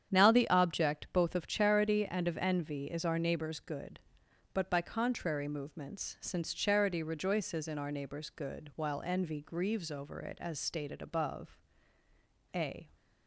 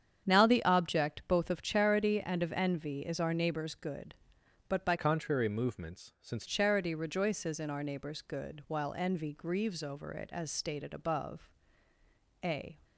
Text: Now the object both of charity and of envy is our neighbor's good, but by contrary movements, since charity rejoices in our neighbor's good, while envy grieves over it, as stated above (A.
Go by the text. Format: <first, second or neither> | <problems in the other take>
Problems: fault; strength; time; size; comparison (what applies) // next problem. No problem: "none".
first | starts louder than the rest; strong; until 1.3 s; 8.5 dB; strong in the first // changes voice from "contrary" to "since"; from 4.9 to 6.4 s; 1.5 s long